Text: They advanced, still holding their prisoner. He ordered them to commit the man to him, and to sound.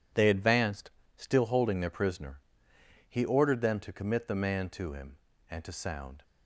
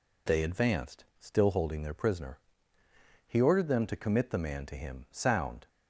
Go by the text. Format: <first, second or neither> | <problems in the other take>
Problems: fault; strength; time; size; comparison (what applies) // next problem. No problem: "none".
first | skips "and to"; at 5.0 s